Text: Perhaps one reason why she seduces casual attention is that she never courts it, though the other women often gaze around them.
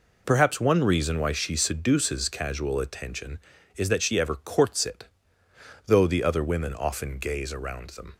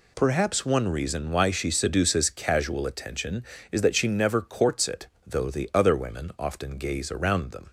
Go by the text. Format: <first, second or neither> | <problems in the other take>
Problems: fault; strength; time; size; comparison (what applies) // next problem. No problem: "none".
second | says "ever" for "never"; at 4.1 s